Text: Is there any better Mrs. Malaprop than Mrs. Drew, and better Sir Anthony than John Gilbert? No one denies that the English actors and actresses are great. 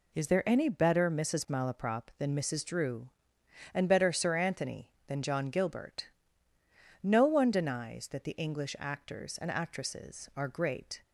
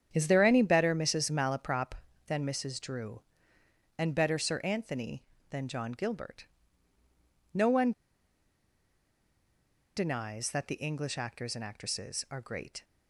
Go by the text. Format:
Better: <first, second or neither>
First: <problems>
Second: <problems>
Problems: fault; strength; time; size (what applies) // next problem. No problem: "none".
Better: first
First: none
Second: starts louder than the rest; strong; until 1.1 s; 9 dB // pauses between "one" and "denies"; strong; at 7.9 s; 2.0 s long